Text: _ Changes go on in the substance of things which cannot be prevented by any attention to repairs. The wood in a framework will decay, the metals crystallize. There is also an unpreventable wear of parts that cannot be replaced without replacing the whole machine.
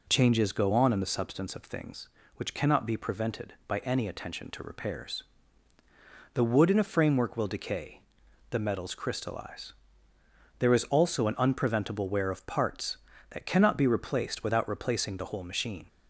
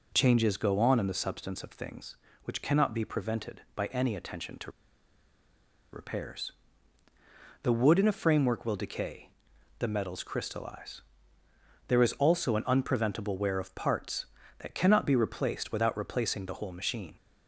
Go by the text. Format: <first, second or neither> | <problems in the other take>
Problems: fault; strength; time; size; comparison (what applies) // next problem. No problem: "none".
first | pauses between "to" and "repairs"; at 4.7 s; 1.2 s long